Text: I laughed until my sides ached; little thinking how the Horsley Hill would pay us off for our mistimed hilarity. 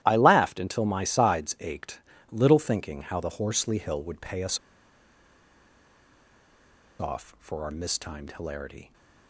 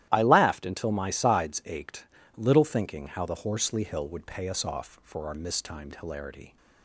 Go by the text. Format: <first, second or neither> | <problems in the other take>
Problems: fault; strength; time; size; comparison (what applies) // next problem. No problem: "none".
second | starts louder than the rest; strong; until 1.0 s; 13 dB; strong in the second // pauses between "us" and "off"; strong; at 4.5 s; 2.4 s long